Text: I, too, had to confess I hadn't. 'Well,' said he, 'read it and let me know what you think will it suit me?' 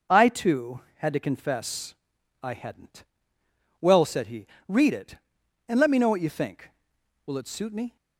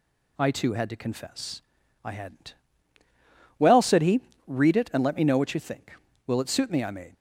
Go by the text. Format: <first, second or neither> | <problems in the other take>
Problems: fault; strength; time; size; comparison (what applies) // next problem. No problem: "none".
first | pauses between "confess" and "I"; at 1.6 s; 0.42 s long; noticeable in the first // goes on to say "I made"; slight; from 6.8 s on; 0.30 s long